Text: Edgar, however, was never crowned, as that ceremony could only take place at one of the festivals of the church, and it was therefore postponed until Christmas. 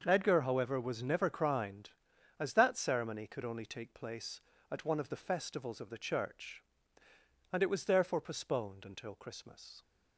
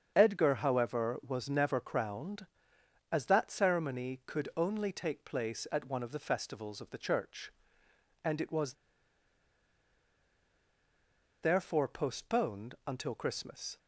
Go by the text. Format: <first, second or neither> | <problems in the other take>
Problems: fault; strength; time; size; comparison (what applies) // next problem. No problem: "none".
first | starts louder than the rest; until 1.1 s; 7 dB; also in the first // pauses between "was" and "therefore"; strong; at 8.7 s; 2.7 s long